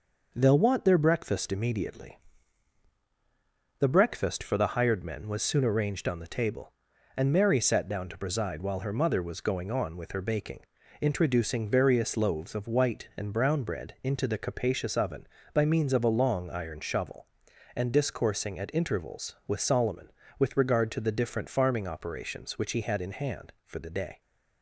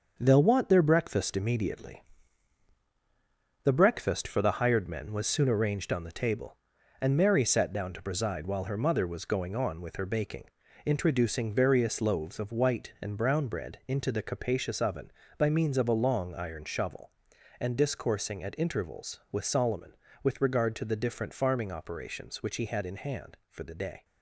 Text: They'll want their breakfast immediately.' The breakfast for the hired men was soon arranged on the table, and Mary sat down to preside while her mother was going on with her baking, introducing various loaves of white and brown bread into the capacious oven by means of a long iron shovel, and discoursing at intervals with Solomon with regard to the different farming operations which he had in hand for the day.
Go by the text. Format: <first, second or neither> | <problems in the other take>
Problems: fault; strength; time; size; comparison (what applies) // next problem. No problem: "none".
first | gets quieter; throughout; 7 dB